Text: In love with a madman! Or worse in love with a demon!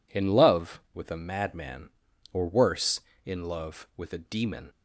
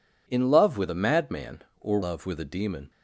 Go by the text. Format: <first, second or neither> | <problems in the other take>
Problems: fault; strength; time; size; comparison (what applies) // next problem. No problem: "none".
first | skips "worse in"; at 2.0 s